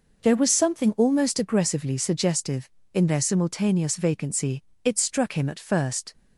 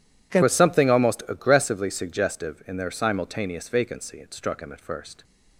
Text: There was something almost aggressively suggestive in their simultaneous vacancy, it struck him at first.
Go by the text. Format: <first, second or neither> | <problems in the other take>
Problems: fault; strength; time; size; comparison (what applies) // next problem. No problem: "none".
first | changes voice at "was"; from 0.4 s on; 4.8 s long